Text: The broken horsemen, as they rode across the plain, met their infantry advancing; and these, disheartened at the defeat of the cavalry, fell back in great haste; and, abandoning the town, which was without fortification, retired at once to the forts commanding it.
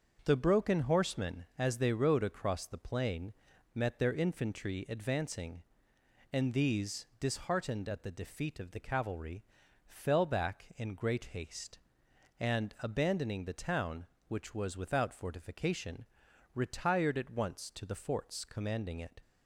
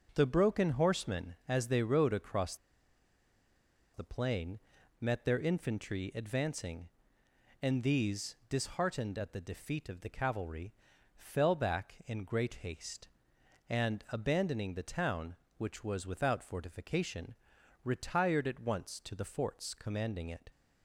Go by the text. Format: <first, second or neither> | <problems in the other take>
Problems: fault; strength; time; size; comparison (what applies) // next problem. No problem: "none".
first | starts louder than the rest; until 1.1 s; 6.5 dB; also in the first // pauses between "across" and "the"; strong; at 2.5 s; 1.3 s long